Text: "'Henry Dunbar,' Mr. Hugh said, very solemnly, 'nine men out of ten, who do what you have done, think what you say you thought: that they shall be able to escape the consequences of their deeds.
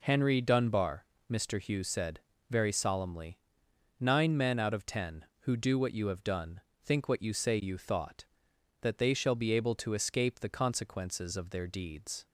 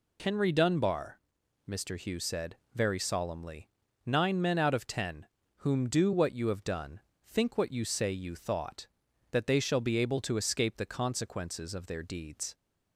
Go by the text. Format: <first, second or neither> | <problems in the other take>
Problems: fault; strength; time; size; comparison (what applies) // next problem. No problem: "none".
first | says "whom" for "who"; at 5.5 s